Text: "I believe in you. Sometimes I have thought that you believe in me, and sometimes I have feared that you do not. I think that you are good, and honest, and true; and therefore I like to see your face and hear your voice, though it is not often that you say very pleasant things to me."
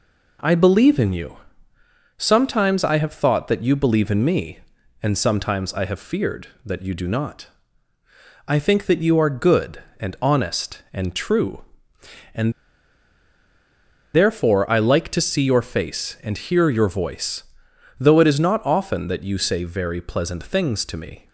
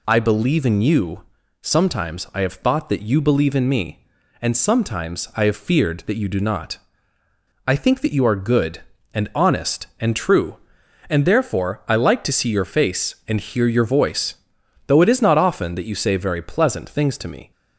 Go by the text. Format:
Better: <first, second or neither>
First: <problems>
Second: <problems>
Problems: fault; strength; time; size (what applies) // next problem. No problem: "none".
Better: second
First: pauses between "and" and "therefore"; strong; at 12.5 s; 1.6 s long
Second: none